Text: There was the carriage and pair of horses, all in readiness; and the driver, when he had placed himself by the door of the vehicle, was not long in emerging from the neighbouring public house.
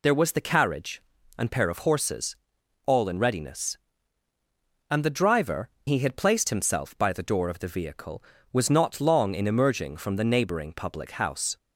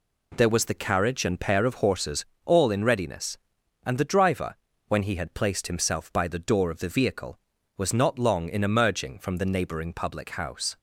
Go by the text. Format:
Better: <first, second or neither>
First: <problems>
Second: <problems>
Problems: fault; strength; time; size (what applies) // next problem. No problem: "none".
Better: second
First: skips "when"; at 5.7 s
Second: none